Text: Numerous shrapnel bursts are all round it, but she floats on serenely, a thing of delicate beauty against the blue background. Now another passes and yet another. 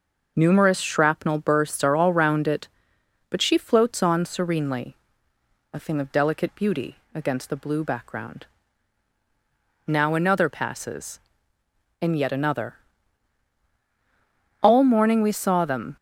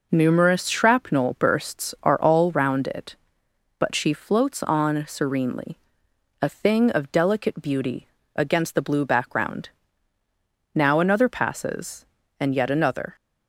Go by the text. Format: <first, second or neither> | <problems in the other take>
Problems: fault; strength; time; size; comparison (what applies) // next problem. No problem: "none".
second | pauses between "beauty" and "against"; slight; at 6.9 s; 0.18 s long; slight in the second // goes on to say "All morning we saw them"; from 14.6 s on; 1.3 s long